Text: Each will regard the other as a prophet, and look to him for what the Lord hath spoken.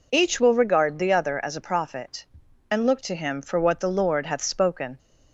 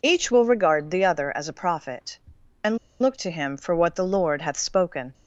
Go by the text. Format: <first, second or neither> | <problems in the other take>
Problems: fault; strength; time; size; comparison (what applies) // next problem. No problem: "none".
first | pauses between "and" and "look"; slight; at 2.7 s; 0.25 s long